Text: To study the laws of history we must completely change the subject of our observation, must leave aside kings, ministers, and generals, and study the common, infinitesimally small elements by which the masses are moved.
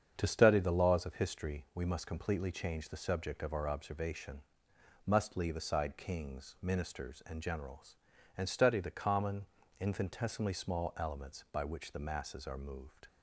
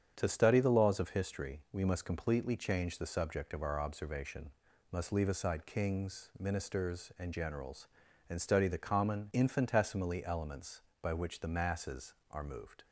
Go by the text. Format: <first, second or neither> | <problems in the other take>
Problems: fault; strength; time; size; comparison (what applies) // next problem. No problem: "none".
first | starts louder than the rest; strong; until 1.1 s; 8 dB; strong in the first // skips "small"; at 10.2 s